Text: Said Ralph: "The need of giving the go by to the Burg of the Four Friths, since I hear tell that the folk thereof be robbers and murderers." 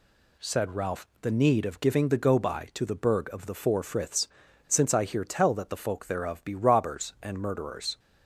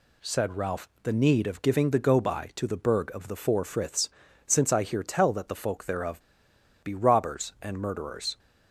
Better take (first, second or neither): first